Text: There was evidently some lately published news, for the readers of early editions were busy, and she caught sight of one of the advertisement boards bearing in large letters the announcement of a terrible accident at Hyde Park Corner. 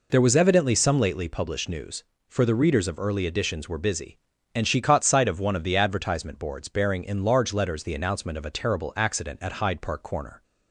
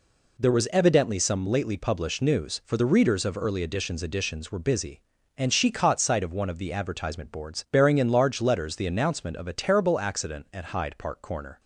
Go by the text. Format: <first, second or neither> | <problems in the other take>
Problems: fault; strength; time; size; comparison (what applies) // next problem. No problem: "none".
first | says "editions" twice; at 4.0 s